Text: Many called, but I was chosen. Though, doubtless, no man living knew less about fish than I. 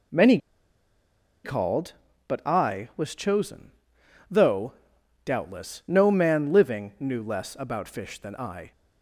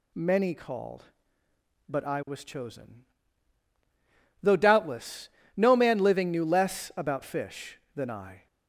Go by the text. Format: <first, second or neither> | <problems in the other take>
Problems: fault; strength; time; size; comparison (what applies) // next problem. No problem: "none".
second | pauses between "Many" and "called"; at 0.3 s; 1.0 s long